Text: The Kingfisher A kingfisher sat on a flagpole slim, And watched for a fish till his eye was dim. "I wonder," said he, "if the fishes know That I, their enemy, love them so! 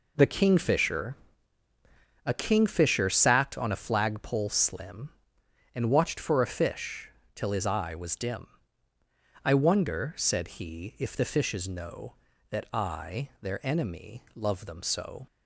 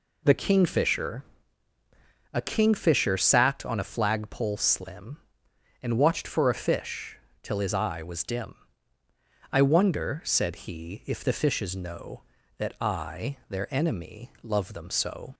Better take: second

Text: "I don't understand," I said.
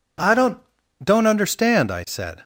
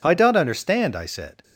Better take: second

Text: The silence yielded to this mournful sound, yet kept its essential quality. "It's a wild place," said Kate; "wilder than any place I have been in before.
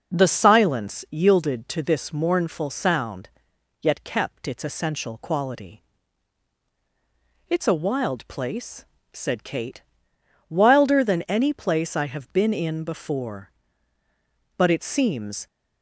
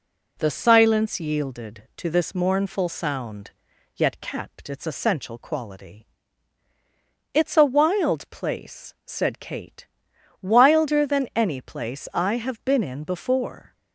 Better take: second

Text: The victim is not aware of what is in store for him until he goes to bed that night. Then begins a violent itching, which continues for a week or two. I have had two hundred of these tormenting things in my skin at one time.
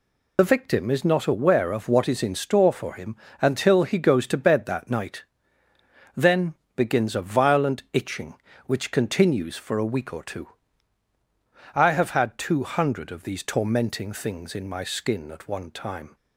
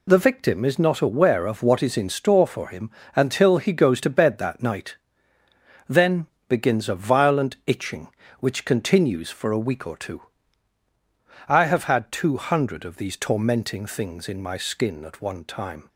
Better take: second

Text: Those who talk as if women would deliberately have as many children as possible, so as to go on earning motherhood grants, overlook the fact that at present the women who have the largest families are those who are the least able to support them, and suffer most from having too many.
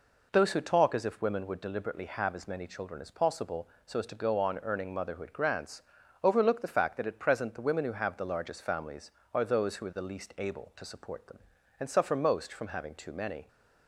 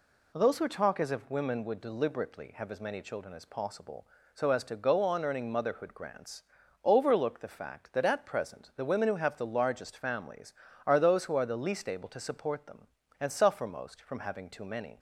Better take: neither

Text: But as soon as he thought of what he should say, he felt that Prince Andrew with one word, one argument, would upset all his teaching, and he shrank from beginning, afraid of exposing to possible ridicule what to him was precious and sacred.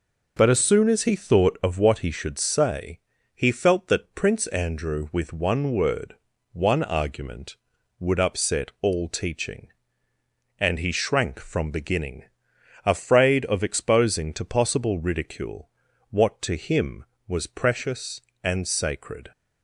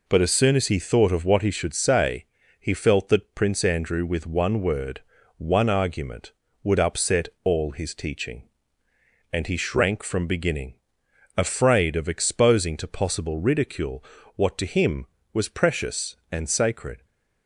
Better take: second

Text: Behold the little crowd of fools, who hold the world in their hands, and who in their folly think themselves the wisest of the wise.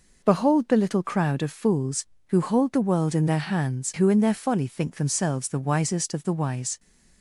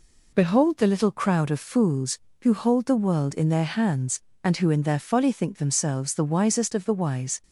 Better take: second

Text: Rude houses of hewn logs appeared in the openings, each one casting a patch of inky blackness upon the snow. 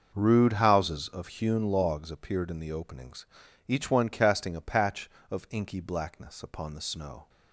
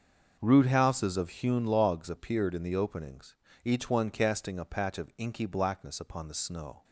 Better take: neither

